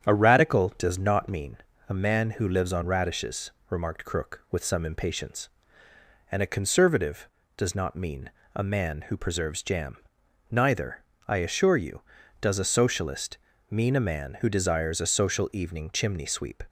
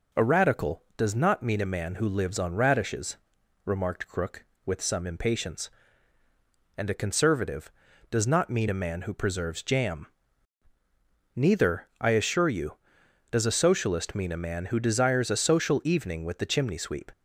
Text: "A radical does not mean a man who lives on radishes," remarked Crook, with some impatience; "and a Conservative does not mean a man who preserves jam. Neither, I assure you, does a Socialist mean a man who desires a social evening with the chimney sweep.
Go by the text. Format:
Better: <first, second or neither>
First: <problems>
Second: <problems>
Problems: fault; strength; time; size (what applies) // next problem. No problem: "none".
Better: second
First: starts louder than the rest; strong; until 1.1 s; 8.5 dB // pauses between "mean" and "a"; slight; at 1.5 s; 0.30 s long // pauses between "mean" and "a"; slight; at 8.2 s; 0.25 s long // pauses between "Socialist" and "mean"; slight; at 13.3 s; 0.32 s long // skips "with the"; at 15.9 s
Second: none